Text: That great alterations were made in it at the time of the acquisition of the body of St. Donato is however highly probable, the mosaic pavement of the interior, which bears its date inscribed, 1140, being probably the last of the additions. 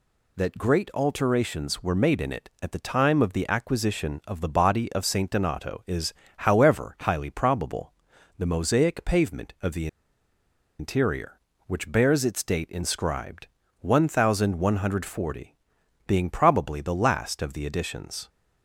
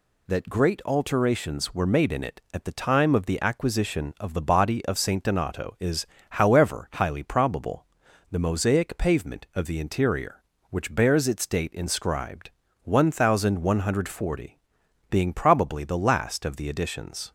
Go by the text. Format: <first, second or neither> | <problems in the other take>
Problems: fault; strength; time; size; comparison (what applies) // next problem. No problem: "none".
second | pauses between "is" and "however"; slight; at 6.1 s; 0.26 s long; slight in the second // pauses between "the" and "interior"; noticeable; at 9.8 s; 0.92 s long